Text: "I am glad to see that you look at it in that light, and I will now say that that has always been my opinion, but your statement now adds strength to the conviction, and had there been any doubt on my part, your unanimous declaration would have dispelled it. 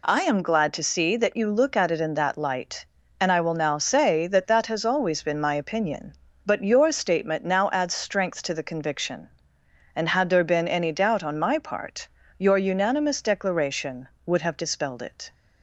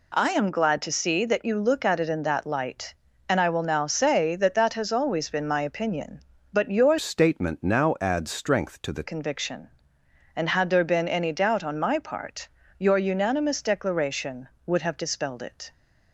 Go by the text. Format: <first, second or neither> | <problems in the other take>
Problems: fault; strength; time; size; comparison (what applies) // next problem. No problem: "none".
first | changes voice from "statement" to "the"; from 6.9 to 9.0 s; 2.1 s long